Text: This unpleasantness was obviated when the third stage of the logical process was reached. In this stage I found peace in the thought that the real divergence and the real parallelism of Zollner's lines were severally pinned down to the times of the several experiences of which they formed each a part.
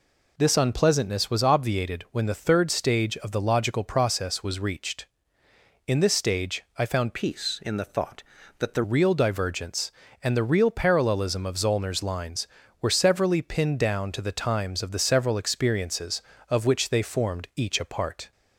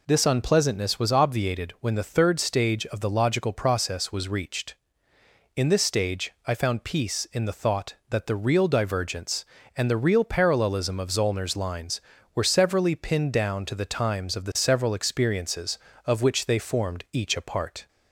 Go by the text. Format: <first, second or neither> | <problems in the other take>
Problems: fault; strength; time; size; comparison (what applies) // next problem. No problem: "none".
second | pauses between "stage" and "I"; slight; at 6.6 s; 0.16 s long; slight in the second // changes voice from "peace" to "the"; from 7.1 to 8.8 s; 1.7 s long